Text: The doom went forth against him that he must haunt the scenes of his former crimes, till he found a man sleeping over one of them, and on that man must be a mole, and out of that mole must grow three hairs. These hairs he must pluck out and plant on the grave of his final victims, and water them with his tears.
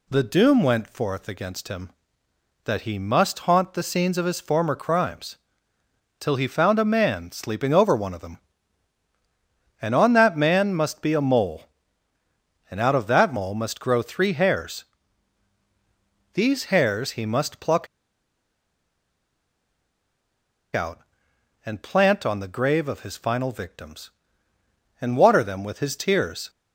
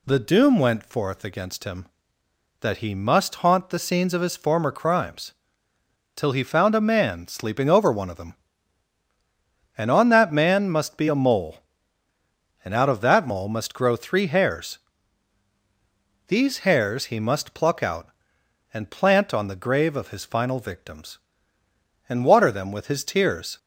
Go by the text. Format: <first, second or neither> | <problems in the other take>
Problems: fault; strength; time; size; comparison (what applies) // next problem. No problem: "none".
second | pauses between "pluck" and "out"; strong; at 17.8 s; 2.8 s long